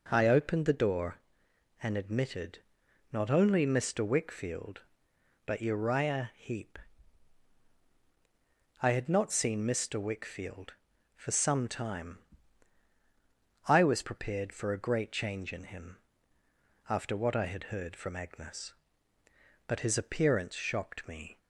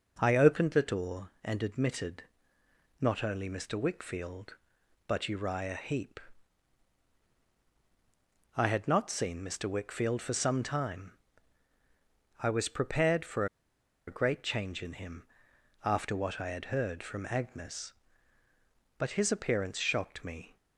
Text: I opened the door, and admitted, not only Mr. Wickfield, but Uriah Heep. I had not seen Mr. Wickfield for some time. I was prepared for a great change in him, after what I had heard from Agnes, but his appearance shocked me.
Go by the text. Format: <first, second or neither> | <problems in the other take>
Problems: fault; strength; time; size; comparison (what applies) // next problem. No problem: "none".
first | pauses between "for" and "a"; noticeable; at 13.4 s; 0.62 s long